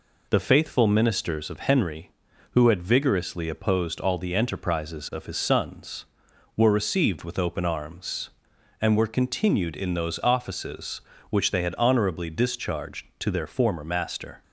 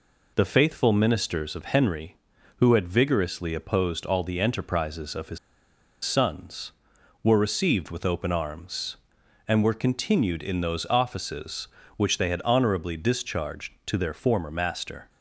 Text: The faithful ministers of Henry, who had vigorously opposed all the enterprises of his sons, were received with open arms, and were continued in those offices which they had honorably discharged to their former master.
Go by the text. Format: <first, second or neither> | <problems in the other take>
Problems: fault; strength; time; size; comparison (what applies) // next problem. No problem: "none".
first | pauses between "his" and "sons"; noticeable; at 5.3 s; 0.66 s long